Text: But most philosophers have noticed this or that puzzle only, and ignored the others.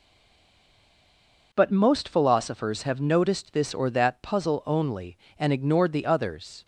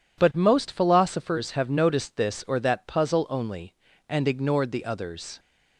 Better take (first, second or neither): second